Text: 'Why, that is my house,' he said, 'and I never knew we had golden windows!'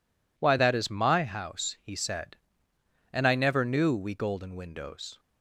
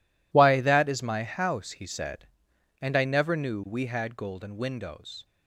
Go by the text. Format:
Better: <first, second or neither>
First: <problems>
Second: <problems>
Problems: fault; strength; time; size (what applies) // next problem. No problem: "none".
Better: second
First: skips "had"; at 4.1 s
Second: none